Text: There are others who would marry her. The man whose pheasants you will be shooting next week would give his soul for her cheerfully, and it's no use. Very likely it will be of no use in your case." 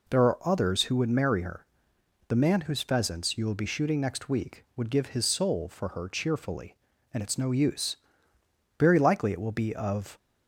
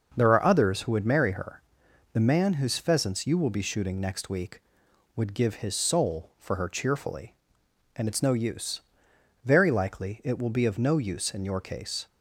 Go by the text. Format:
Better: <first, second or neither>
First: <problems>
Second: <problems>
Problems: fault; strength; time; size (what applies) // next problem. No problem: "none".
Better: second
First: stops before "no use in your case"; at 10.1 s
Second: none